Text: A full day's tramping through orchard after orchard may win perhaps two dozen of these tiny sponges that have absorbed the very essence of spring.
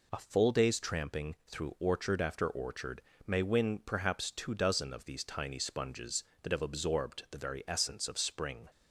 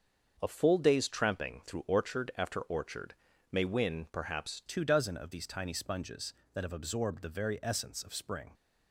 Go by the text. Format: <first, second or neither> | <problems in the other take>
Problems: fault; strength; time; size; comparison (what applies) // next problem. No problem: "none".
first | starts louder than the rest; until 1.4 s; 6.5 dB // pauses between "orchard" and "may"; slight; at 3.1 s; 0.36 s long; slight in the first // changes voice at "two"; from 4.6 s on; 3.9 s long